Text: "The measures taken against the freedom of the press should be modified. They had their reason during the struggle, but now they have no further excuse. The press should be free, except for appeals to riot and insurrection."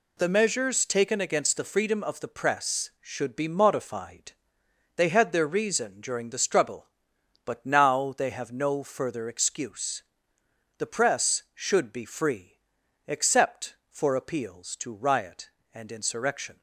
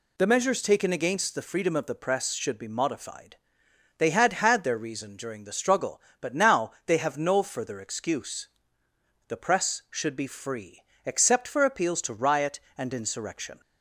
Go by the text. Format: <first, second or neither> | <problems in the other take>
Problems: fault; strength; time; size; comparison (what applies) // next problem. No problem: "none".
first | says "had" twice; at 4.3 s // pauses between "now" and "they"; slight; at 6.7 s; 0.16 s long